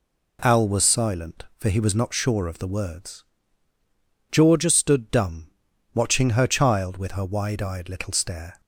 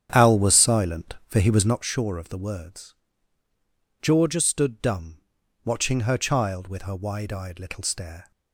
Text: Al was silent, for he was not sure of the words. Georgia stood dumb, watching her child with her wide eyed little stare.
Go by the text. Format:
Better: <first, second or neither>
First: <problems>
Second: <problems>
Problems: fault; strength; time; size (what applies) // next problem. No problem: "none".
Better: first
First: none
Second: starts louder than the rest; strong; until 1.8 s; 9 dB